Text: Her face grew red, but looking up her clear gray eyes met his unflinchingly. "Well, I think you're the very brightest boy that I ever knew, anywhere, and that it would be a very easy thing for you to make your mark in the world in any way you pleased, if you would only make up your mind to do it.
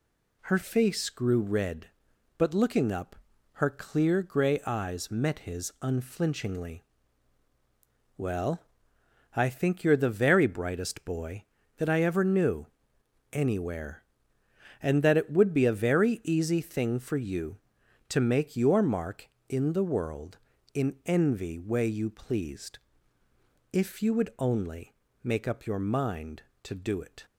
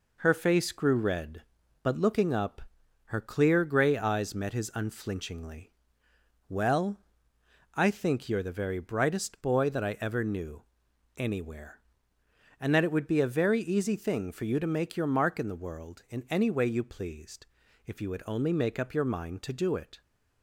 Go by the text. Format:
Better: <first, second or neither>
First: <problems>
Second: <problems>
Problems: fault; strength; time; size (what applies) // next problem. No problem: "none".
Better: second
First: pauses between "up" and "her"; at 3.1 s; 0.38 s long // says "envy" for "any"; at 21.0 s // pauses between "only" and "make"; slight; at 24.9 s; 0.26 s long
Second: pauses between "up" and "her"; at 2.6 s; 0.44 s long